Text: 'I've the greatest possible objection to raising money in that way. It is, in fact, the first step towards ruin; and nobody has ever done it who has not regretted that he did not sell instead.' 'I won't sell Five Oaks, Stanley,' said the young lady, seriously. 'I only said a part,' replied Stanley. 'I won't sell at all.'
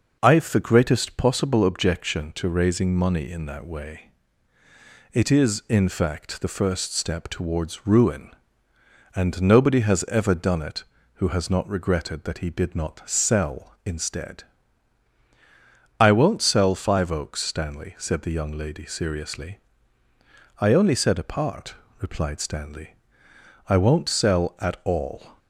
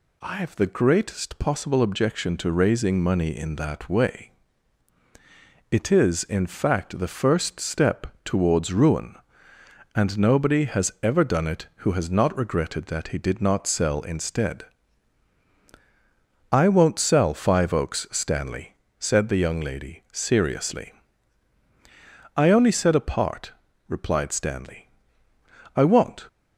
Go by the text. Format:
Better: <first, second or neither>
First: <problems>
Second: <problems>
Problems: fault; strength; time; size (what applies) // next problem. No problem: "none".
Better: first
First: none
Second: pauses between "step" and "towards"; slight; at 8.0 s; 0.16 s long // stops before "sell at all"; at 26.2 s